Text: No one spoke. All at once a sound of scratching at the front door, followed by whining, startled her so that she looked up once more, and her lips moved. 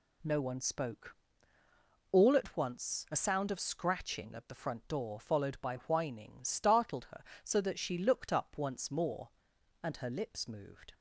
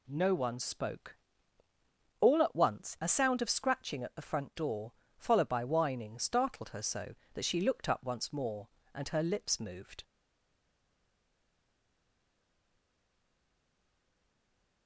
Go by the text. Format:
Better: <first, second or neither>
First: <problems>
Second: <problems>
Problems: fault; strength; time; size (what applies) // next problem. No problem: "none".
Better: first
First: none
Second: stays silent after the last word; strong; from 10.0 s on; 4.8 s long